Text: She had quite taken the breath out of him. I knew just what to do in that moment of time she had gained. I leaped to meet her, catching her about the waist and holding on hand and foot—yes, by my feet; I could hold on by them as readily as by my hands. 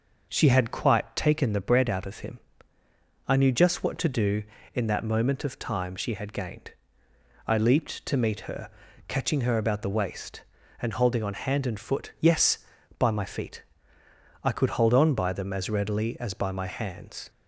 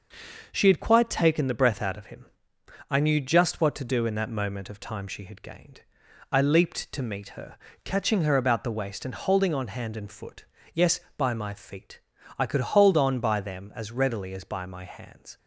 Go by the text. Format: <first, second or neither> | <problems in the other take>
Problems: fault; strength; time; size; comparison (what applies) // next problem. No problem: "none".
second | says "bread" for "breath"; at 1.5 s